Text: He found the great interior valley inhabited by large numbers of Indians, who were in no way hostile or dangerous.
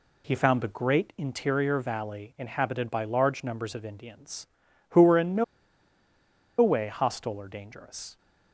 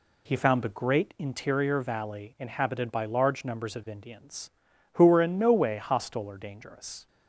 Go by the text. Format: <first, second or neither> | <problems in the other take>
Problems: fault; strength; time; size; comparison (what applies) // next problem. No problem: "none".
second | pauses between "no" and "way"; at 5.4 s; 1.1 s long